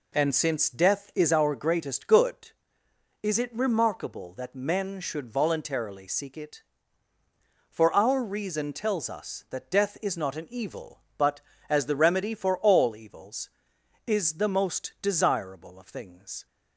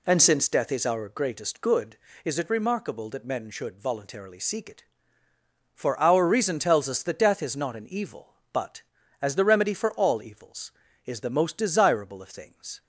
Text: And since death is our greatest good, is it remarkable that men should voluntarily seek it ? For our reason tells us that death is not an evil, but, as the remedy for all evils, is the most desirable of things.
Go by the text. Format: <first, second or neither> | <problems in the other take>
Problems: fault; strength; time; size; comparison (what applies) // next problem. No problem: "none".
neither | none